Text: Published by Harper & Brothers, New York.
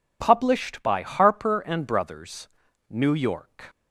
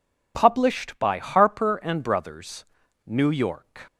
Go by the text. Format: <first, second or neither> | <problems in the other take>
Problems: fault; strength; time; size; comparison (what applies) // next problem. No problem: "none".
neither | none